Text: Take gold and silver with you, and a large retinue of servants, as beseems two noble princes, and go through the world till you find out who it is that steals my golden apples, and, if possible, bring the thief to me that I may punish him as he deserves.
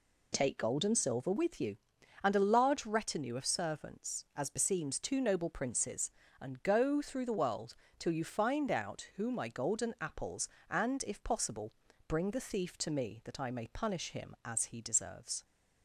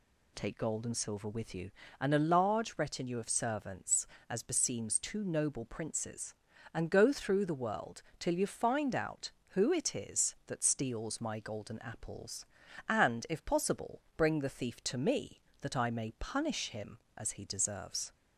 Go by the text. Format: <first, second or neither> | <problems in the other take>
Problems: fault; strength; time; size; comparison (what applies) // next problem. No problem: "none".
second | pauses between "world" and "till"; slight; at 7.7 s; 0.24 s long; slight in the second // skips "it is that steals"; at 9.3 s